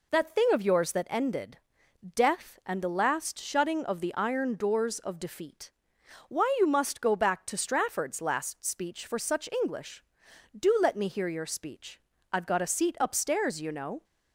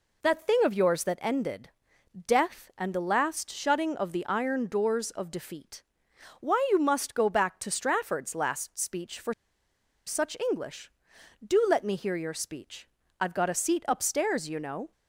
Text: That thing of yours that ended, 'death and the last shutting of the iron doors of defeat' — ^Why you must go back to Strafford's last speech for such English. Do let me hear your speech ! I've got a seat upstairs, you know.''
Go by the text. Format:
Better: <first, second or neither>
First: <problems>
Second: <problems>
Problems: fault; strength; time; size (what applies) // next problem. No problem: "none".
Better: first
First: none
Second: pauses between "for" and "such"; noticeable; at 9.3 s; 0.74 s long